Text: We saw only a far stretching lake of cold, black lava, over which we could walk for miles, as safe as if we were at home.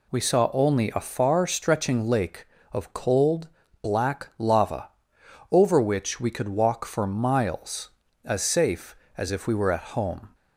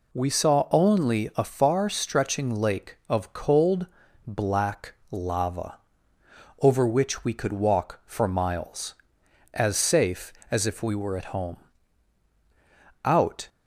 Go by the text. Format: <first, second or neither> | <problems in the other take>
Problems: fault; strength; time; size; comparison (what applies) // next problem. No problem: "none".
first | pauses between "black" and "lava"; slight; at 4.9 s; 0.16 s long // goes on to say "Out"; slight; from 13.0 s on; 0.44 s long